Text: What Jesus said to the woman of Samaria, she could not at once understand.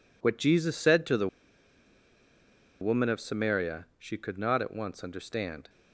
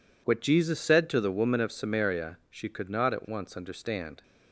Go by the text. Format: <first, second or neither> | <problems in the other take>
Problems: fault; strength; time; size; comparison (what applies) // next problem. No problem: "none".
second | pauses between "the" and "woman"; strong; at 1.2 s; 1.5 s long